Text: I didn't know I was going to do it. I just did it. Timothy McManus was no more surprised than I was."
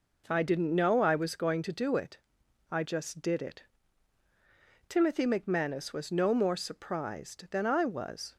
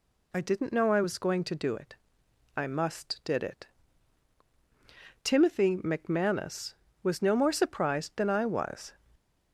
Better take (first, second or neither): first